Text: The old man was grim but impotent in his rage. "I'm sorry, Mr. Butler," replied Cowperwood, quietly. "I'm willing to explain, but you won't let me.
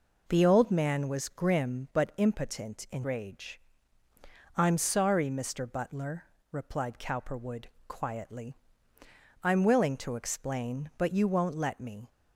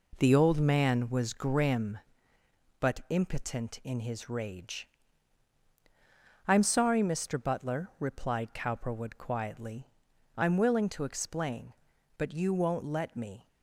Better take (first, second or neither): second